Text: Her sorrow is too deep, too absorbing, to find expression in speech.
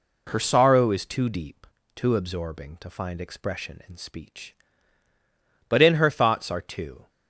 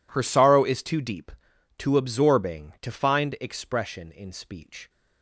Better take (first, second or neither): second